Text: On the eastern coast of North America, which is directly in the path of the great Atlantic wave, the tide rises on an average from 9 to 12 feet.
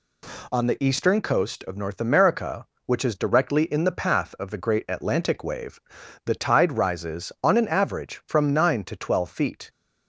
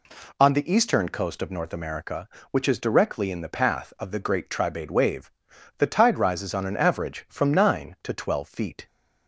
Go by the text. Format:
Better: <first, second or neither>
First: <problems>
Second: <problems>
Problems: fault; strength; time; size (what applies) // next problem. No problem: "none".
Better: first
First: none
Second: says "Tribade" for "Atlantic"; at 4.4 s